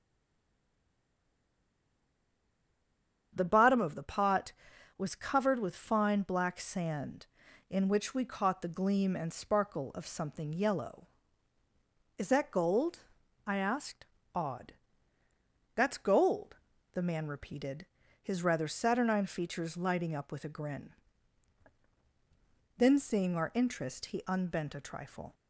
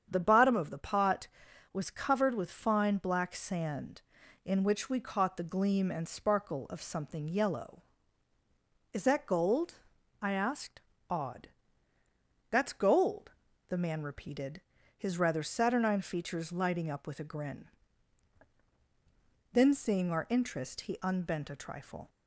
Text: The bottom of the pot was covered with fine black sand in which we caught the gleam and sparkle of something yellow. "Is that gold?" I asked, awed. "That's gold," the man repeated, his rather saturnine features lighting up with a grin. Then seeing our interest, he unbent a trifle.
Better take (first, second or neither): second